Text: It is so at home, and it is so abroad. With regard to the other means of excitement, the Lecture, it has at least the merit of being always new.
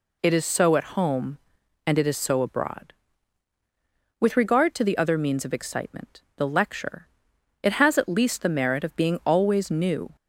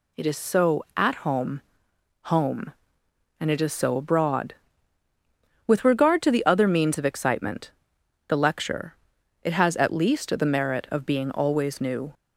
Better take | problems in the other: first | says "home" twice; at 2.2 s

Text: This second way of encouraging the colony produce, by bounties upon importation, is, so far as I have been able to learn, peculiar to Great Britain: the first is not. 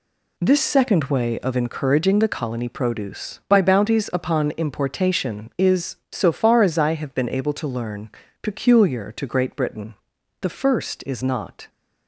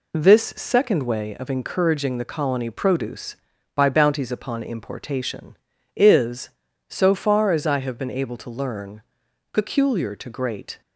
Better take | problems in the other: first | stops before "Britain the first is not"; at 10.8 s

